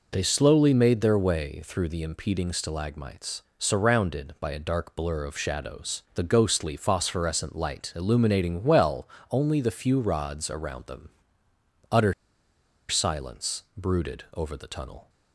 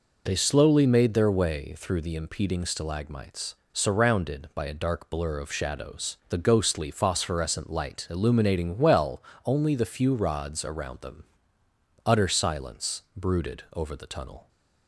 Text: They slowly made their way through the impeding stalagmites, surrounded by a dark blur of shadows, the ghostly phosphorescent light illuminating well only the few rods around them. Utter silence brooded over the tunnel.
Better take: second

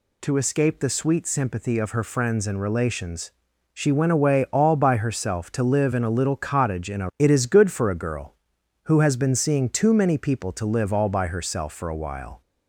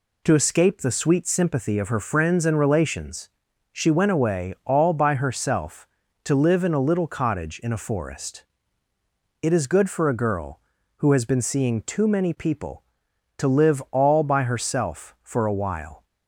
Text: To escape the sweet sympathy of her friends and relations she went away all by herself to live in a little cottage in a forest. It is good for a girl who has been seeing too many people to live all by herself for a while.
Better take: second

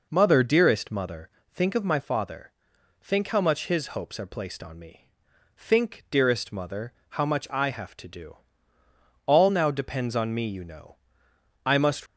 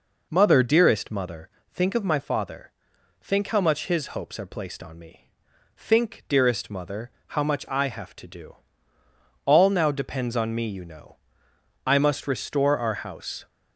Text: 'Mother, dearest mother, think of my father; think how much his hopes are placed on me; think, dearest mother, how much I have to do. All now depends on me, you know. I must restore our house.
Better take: second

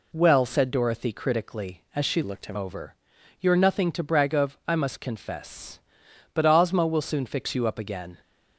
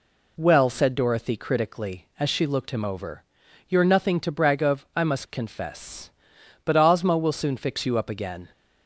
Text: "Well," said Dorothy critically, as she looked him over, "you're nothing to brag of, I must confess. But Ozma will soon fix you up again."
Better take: second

